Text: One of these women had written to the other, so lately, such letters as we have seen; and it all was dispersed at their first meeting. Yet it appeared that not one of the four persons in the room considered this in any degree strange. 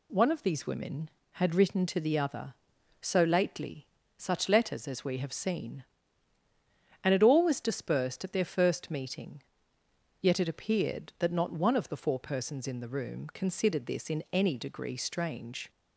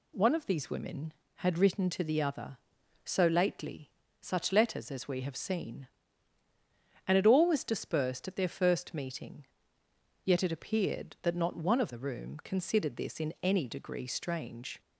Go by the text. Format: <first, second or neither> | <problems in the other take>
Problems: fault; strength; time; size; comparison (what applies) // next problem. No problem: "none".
first | skips "the four persons in"; at 11.9 s